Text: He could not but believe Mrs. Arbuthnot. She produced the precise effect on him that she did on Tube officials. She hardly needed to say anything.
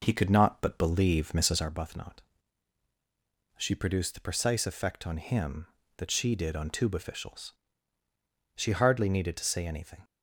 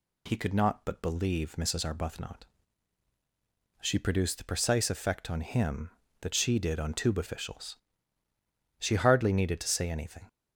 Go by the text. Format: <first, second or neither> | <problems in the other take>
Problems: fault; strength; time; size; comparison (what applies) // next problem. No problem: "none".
second | starts louder than the rest; noticeable; until 1.7 s; 5 dB